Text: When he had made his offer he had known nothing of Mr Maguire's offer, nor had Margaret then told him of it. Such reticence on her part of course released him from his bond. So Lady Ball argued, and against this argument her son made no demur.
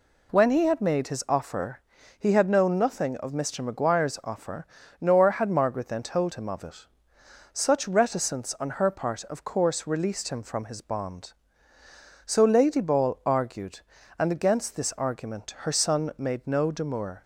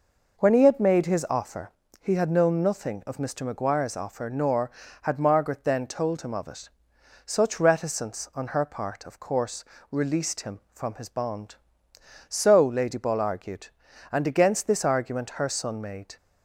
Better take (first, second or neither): first